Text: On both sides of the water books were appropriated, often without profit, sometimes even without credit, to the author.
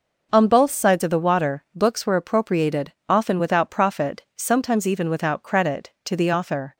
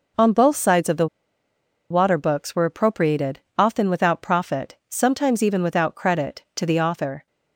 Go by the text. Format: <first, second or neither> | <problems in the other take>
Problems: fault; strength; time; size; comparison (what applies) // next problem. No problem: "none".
first | pauses between "the" and "water"; noticeable; at 1.0 s; 0.82 s long